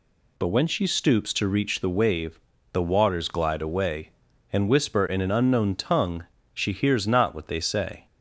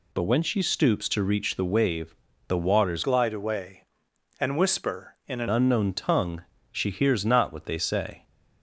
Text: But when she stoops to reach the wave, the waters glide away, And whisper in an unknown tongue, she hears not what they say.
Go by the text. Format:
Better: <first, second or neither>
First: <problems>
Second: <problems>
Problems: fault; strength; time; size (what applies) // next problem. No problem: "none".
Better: first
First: none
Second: changes voice from "glide" to "an"; from 3.0 to 5.4 s; 2.4 s long